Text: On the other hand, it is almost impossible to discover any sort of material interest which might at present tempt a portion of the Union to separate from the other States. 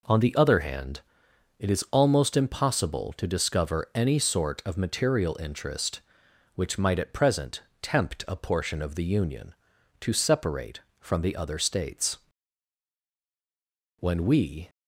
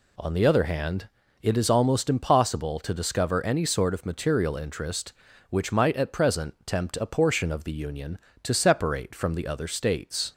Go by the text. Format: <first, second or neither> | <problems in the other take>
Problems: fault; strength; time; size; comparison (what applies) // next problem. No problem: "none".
second | pauses between "present" and "tempt"; slight; at 7.6 s; 0.20 s long // goes on to say "When we"; noticeable; from 13.9 s on; 0.70 s long